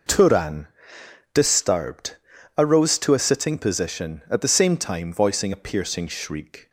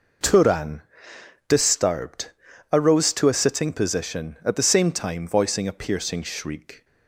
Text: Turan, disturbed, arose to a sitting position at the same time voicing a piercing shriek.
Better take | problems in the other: neither | none

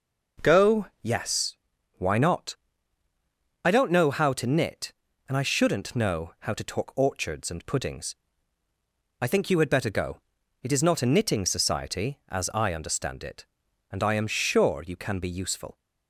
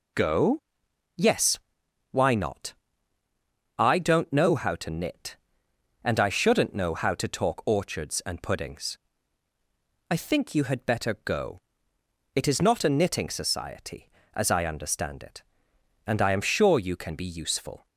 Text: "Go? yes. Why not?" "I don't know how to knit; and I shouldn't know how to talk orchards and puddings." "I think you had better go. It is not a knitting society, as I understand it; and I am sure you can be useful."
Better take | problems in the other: neither | none

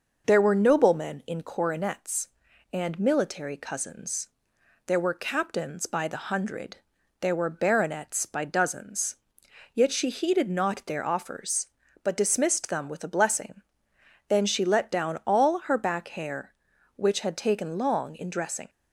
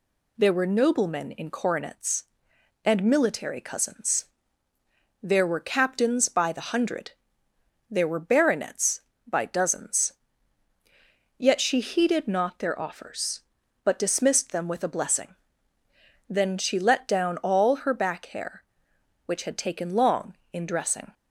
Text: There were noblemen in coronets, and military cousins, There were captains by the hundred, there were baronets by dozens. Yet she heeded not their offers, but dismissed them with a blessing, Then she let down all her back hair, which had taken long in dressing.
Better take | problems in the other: neither | none

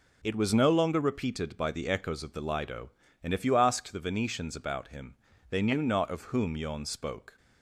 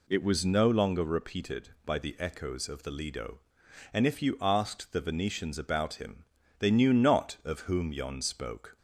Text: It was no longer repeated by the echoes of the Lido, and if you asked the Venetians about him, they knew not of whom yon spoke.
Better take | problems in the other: neither | none

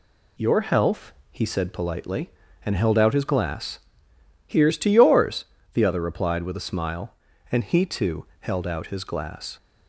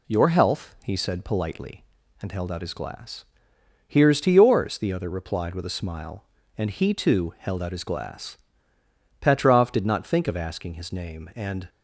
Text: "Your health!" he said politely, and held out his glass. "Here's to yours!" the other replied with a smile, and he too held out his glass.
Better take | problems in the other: first | goes on to say "Petrov did not think of asking his name and"; strong; from 9.2 s on; 2.4 s long

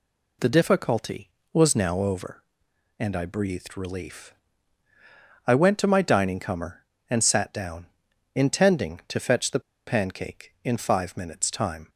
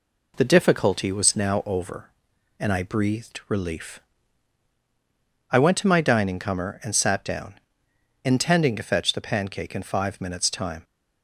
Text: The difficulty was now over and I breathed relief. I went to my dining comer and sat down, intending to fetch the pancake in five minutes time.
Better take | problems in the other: second | pauses between "the" and "pancake"; slight; at 9.5 s; 0.27 s long

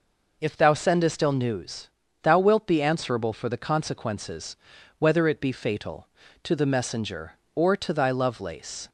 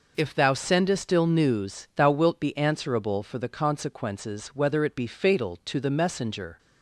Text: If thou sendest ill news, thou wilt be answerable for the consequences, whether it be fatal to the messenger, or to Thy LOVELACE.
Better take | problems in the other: first | stops before "or to Thy LOVELACE"; at 6.5 s

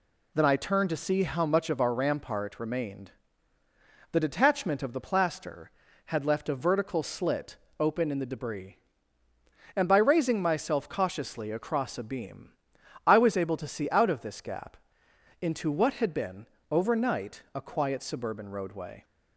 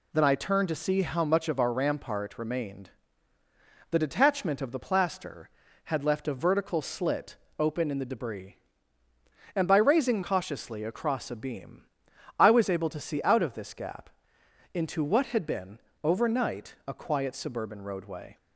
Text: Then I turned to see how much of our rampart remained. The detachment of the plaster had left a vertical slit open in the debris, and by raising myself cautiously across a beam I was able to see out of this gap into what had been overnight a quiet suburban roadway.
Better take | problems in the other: first | pauses between "slit" and "open"; slight; at 7.3 s; 0.22 s long; slight in the first // skips "myself"; at 10.2 s // pauses between "beam" and "I"; noticeable; at 11.8 s; 0.54 s long; noticeable in the first // pauses between "gap" and "into"; noticeable; at 14.0 s; 0.64 s long; noticeable in the first // pauses between "been" and "overnight"; slight; at 15.7 s; 0.24 s long; slight in the first

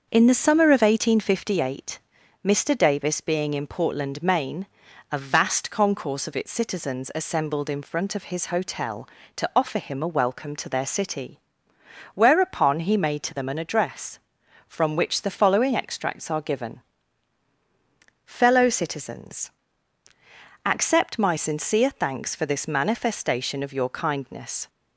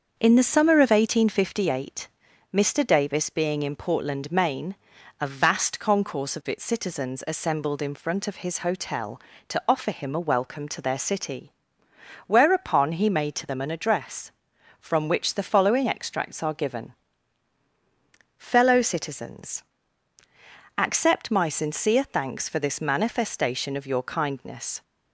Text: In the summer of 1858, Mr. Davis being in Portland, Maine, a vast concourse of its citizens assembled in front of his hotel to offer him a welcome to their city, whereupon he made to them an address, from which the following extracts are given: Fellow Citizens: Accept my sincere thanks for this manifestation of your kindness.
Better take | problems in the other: neither | starts louder than the rest; the same in both

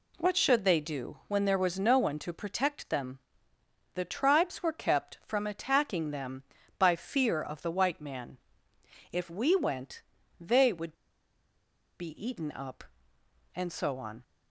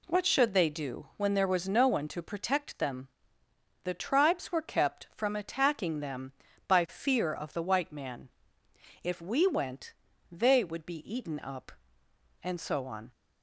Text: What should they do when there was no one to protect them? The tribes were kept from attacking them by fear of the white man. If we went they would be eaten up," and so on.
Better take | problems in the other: second | pauses between "went" and "they"; slight; at 10.0 s; 0.36 s long; slight in the second // pauses between "would" and "be"; at 10.9 s; 1.0 s long

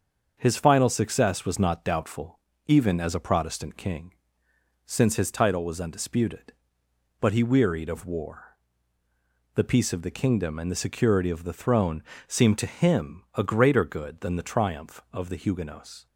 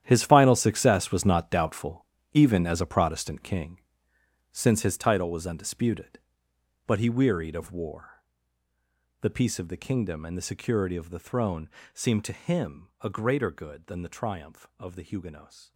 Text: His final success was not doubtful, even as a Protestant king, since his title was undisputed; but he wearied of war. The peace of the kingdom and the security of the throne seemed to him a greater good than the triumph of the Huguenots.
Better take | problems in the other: first | gets quieter; strong; throughout; 14.5 dB // starts louder than the rest; strong; until 1.0 s; 11 dB; also in the first // pauses between "throne" and "seemed"; slight; at 11.7 s; 0.24 s long; slight in the first

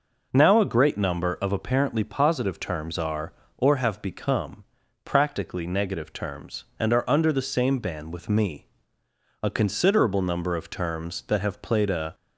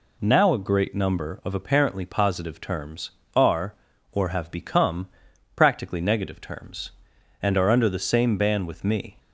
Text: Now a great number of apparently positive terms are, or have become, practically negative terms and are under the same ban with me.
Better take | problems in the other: second | goes on to say "A considerable number of terms that have played a"; strong; from 9.4 s on; 2.7 s long

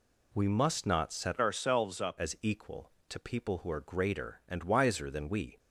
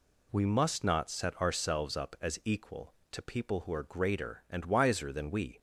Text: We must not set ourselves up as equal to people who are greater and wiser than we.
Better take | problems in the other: second | changes voice from "ourselves" to "up"; from 1.3 to 2.1 s; 0.8 s long

